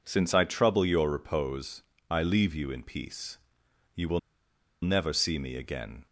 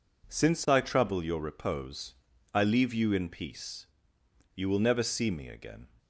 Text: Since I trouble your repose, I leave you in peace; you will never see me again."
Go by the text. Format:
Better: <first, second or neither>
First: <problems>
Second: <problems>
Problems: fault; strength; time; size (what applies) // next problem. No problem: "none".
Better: second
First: pauses between "will" and "never"; noticeable; at 4.1 s; 0.63 s long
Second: none